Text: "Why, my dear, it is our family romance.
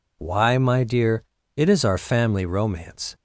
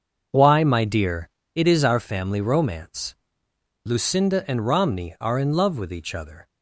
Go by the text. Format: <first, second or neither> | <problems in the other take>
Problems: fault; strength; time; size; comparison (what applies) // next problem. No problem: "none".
first | starts louder than the rest; until 1.5 s; 6.5 dB // goes on to say "Lucinda and Romney are in love with each other"; strong; from 3.8 s on; 2.6 s long